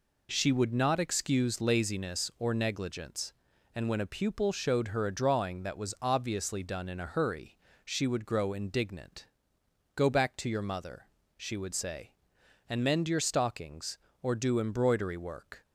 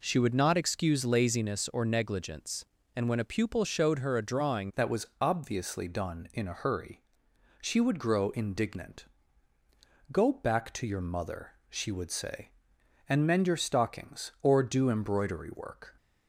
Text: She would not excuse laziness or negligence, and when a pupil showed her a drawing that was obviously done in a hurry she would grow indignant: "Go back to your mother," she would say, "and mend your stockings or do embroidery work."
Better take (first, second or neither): first